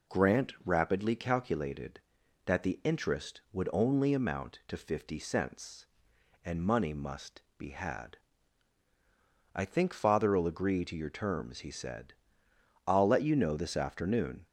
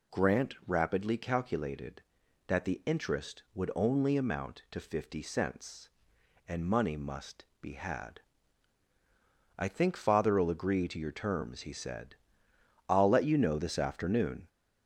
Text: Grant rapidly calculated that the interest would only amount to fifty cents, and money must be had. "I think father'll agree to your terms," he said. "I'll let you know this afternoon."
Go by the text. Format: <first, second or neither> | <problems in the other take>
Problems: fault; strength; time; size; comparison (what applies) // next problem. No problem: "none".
first | gets louder; slight; throughout; 2.5 dB // pauses between "must" and "be"; slight; at 7.4 s; 0.16 s long; slight in the first